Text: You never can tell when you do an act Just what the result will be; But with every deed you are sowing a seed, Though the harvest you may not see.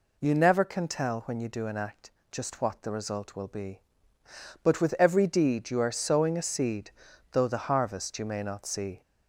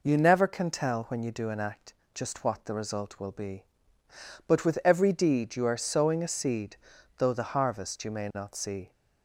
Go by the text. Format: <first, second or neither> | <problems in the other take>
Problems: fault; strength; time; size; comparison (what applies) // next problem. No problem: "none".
second | gets louder; slight; throughout; 2 dB // pauses between "act" and "Just"; slight; at 2.0 s; 0.22 s long; slight in the second